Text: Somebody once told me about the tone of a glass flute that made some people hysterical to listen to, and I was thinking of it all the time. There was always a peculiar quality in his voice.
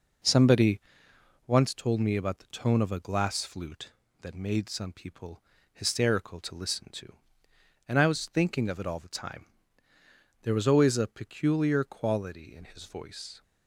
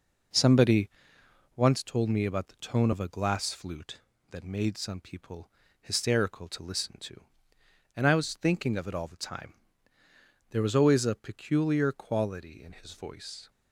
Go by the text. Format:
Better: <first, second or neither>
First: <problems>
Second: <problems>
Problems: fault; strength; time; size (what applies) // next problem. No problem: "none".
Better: neither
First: pauses between "Somebody" and "once"; noticeable; at 0.7 s; 0.70 s long // pauses between "people" and "hysterical"; slight; at 5.4 s; 0.32 s long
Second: pauses between "Somebody" and "once"; noticeable; at 0.8 s; 0.70 s long // pauses between "people" and "hysterical"; slight; at 5.4 s; 0.32 s long